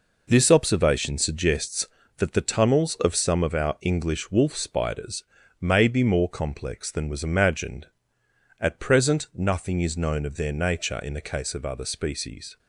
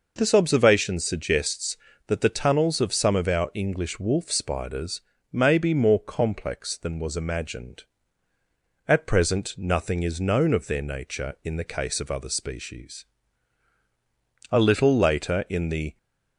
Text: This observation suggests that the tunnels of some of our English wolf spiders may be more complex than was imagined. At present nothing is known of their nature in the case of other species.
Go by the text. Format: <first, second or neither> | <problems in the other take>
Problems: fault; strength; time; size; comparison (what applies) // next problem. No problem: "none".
first | pauses between "spiders" and "may"; slight; at 5.0 s; 0.30 s long; slight in the first // goes on to say "A little later in the"; from 14.5 s on; 1.4 s long